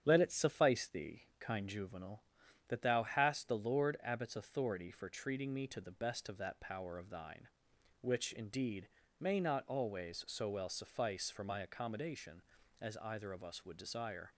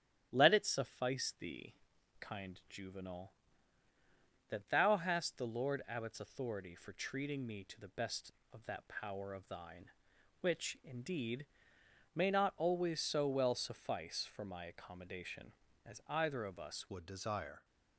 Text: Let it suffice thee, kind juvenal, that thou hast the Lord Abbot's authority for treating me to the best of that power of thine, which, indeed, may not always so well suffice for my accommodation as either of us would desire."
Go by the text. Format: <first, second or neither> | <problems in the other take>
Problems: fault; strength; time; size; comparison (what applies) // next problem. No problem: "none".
first | starts louder than the rest; strong; until 1.3 s; 11 dB; strong in the first // changes voice at "would"; from 16.9 s on; 0.7 s long